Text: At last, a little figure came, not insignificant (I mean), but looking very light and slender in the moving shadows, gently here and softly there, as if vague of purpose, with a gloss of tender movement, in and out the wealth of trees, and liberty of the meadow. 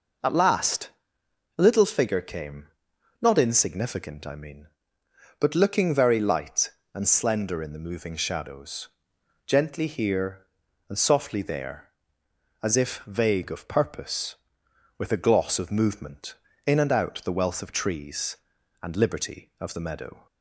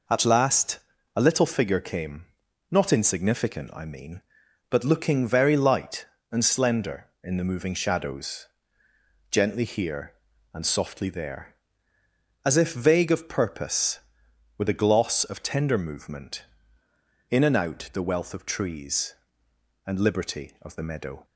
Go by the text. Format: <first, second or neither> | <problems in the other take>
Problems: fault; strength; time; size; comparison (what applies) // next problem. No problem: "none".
second | skips "tender"; at 15.7 s